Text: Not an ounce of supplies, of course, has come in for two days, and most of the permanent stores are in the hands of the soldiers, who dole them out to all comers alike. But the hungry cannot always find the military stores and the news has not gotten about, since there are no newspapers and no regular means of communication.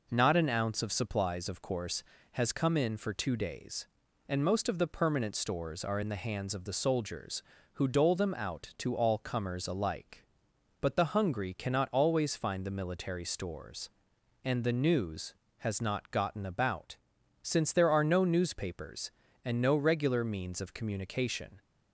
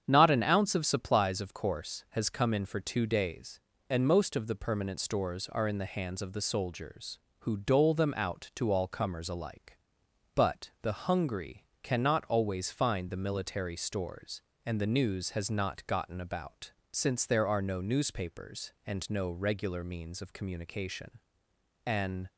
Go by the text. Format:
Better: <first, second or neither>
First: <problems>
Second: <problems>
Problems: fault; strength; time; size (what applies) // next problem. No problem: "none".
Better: first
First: none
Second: starts louder than the rest; strong; until 1.0 s; 8.5 dB // pauses between "hungry" and "cannot"; slight; at 11.6 s; 0.18 s long // goes on to say "An"; slight; from 21.8 s on; 0.42 s long